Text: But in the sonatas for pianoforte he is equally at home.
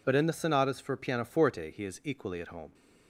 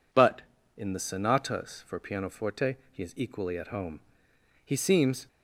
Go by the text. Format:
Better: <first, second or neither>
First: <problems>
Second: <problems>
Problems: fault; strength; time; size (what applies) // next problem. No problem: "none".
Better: first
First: none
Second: pauses between "pianoforte" and "he"; slight; at 2.7 s; 0.16 s long // goes on to say "He seems"; noticeable; from 4.6 s on; 0.64 s long